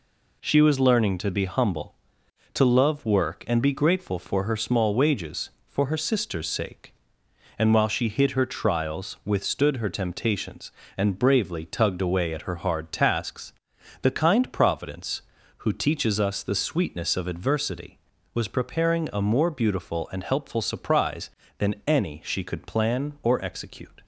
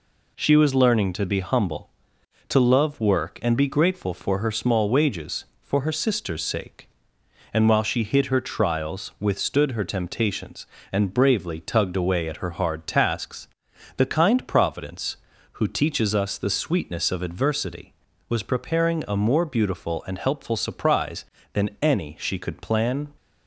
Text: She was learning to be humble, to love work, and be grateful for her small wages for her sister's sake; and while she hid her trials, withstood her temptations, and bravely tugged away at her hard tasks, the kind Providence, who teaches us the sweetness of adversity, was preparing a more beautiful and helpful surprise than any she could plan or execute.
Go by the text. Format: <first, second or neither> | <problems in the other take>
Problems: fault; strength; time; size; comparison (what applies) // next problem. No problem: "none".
first | stops before "or execute"; at 23.1 s